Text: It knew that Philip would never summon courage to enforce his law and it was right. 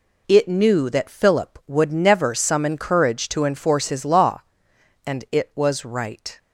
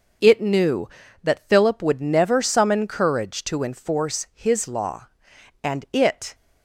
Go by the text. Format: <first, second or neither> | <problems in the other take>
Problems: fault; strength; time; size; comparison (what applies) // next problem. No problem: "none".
first | stops before "was right"; at 6.3 s